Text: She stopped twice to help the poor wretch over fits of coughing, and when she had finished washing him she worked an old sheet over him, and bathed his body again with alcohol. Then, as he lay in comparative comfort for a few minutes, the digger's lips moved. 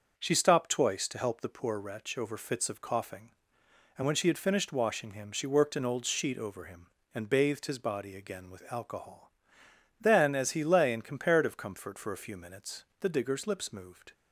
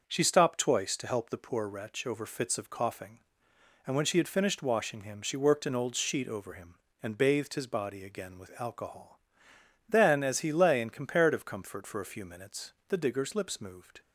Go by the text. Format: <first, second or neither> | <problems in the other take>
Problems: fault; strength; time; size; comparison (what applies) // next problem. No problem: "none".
neither | starts louder than the rest; the same in both